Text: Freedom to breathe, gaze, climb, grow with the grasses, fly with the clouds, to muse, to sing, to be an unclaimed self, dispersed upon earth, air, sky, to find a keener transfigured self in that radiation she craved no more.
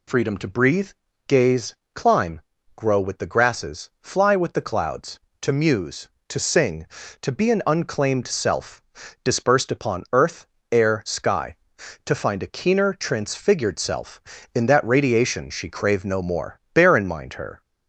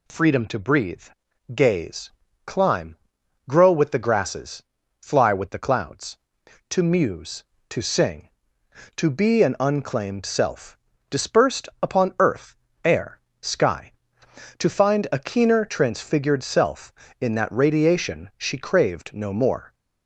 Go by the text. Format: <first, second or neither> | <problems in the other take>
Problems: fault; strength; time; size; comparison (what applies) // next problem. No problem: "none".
second | goes on to say "Bear in mind her"; noticeable; from 16.7 s on; 0.88 s long